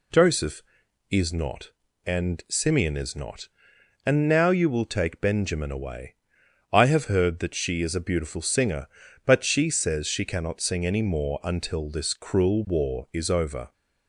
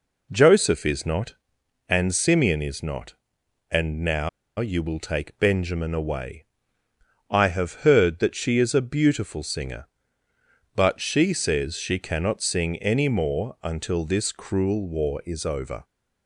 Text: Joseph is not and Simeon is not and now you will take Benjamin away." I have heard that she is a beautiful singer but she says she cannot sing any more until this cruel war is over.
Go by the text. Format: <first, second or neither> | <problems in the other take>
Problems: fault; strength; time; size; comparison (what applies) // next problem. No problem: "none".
first | pauses between "now" and "you"; slight; at 4.2 s; 0.30 s long